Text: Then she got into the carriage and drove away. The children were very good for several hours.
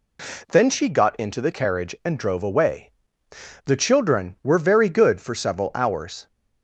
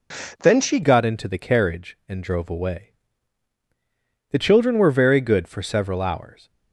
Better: first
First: none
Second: changes voice at "got"; from 0.8 s on; 5.6 s long

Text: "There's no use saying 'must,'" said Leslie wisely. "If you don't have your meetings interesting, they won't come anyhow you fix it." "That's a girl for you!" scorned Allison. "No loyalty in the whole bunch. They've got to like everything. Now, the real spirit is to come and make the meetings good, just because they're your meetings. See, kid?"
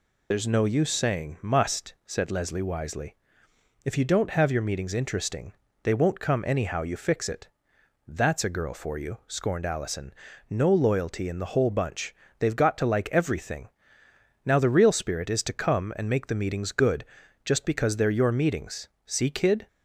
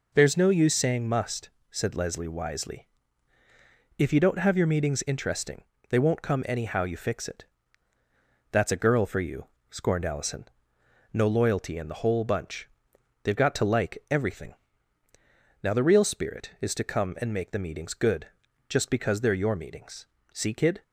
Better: second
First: loses the start of "There's"; at 0.3 s; 50 ms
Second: none

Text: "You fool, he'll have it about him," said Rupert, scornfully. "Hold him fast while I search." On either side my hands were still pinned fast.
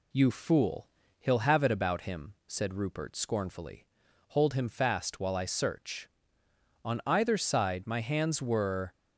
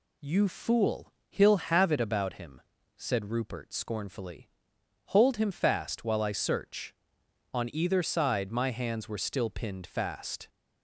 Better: second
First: stops before "still pinned fast"; at 8.9 s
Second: none

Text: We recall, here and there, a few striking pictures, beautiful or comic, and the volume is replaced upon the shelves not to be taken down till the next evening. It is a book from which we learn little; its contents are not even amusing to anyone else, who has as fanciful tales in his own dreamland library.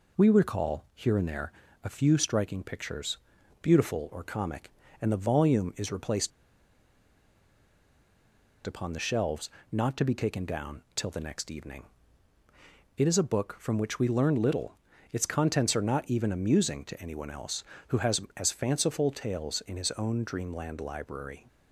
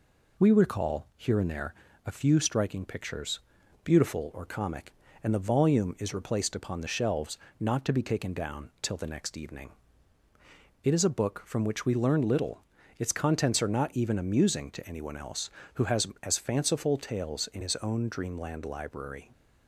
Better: second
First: pauses between "replaced" and "upon"; strong; at 6.3 s; 2.3 s long // pauses between "shelves" and "not"; slight; at 9.5 s; 0.20 s long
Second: pauses between "shelves" and "not"; slight; at 7.3 s; 0.20 s long

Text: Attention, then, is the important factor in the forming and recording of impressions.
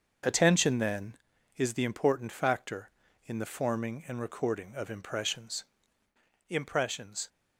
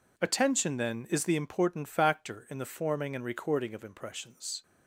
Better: second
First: starts louder than the rest; until 1.7 s; 6.5 dB // says "impressions" twice; at 6.4 s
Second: none

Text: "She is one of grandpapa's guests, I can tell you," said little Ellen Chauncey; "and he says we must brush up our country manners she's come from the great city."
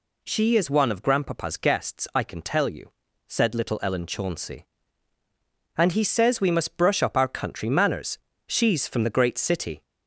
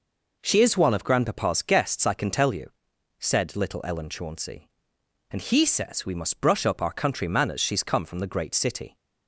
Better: second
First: pauses between "manners" and "she's"; slight; at 8.1 s; 0.28 s long // skips "come"; at 8.8 s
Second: none

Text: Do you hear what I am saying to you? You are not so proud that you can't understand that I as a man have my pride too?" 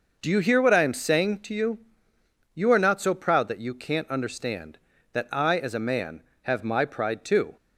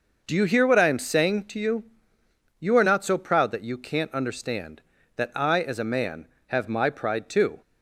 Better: neither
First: none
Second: none

